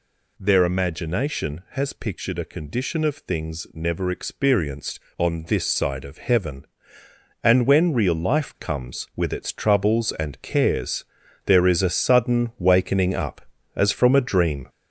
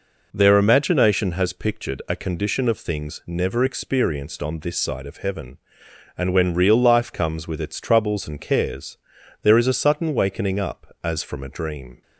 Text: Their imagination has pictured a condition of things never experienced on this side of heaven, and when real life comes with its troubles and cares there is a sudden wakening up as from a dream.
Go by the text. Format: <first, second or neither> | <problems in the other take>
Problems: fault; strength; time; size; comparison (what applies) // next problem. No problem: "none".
second | gets louder; noticeable; throughout; 6 dB // pauses between "cares" and "there"; at 11.0 s; 0.42 s long; also in the second